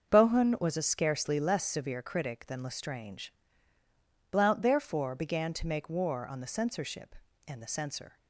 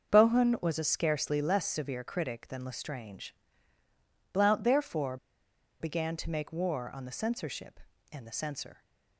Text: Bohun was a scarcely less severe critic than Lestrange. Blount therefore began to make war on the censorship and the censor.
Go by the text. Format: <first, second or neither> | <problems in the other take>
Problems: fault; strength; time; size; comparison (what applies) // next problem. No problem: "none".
first | starts louder than the rest; until 1.1 s; 6.5 dB; also in the first // pauses between "therefore" and "began"; noticeable; at 5.1 s; 0.64 s long